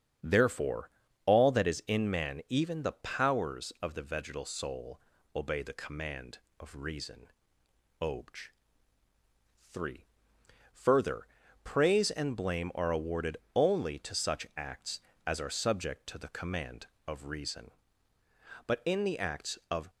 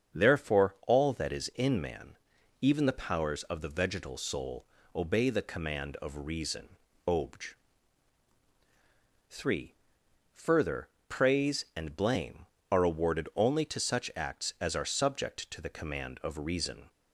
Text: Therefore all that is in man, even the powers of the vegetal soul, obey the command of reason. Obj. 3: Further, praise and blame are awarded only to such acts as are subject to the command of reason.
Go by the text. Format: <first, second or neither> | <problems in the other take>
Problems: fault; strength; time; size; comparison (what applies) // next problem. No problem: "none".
second | starts louder than the rest; strong; until 1.5 s; 7.5 dB; strong in the second // pauses between "Therefore" and "all"; at 0.8 s; 0.36 s long // pauses between "awarded" and "only"; slight; at 13.3 s; 0.18 s long // goes on to say "But in the acts of"; noticeable; from 18.6 s on; 1.2 s long